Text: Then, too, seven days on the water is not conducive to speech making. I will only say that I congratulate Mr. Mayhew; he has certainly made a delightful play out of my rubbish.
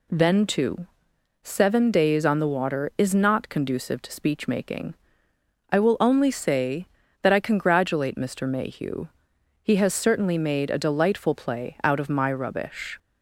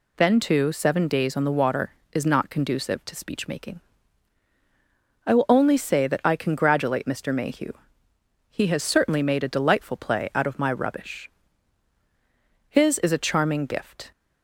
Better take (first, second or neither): first